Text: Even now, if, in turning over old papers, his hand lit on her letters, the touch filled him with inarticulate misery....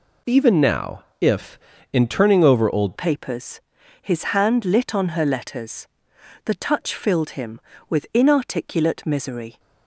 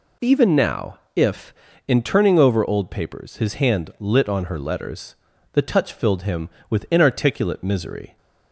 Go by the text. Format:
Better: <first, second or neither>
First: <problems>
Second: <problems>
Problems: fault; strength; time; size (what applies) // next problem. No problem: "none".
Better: second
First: changes voice at "papers"; from 2.9 s on; 6.6 s long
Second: none